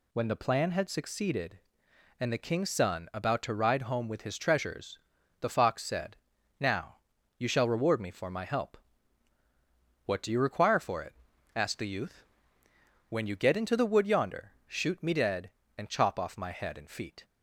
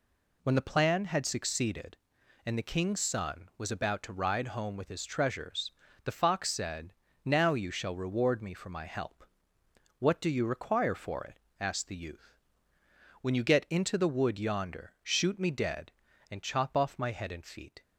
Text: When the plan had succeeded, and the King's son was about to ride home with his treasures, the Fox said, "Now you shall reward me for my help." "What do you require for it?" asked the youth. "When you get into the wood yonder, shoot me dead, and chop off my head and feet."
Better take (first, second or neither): second